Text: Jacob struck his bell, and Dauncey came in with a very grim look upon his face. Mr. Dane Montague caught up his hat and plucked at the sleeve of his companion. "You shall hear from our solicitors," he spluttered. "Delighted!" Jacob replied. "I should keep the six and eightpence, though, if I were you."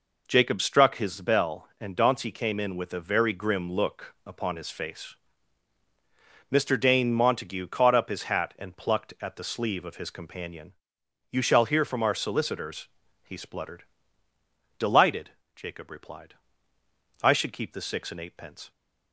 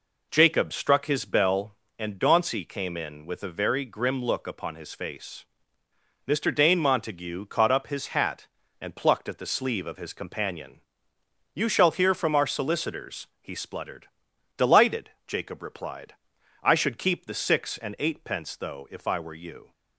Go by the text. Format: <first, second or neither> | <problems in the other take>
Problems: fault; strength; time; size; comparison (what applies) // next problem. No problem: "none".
second | stops before "though if I were you"; at 18.7 s